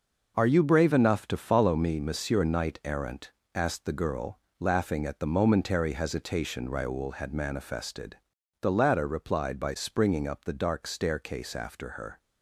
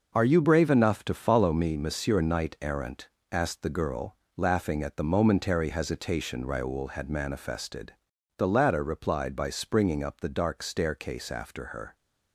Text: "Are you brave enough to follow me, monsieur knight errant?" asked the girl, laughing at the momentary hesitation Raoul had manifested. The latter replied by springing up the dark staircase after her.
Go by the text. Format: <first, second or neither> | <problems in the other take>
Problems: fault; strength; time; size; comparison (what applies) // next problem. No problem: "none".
neither | none